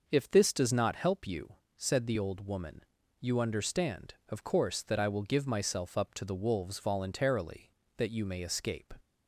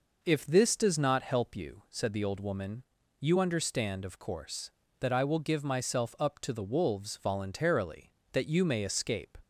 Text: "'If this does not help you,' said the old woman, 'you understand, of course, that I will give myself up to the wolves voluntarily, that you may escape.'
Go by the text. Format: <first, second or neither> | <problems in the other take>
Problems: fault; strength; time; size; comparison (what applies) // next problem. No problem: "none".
neither | none